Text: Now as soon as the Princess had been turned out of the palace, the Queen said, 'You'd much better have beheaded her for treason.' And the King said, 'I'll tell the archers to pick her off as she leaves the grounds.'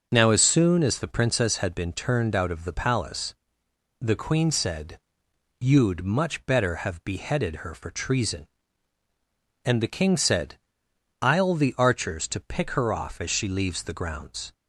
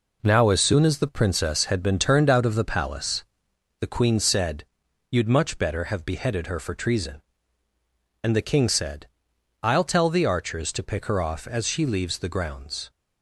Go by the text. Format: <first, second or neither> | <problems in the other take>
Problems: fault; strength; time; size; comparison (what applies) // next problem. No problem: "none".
second | starts louder than the rest; until 1.1 s; 6.5 dB // skips "tell"; at 11.5 s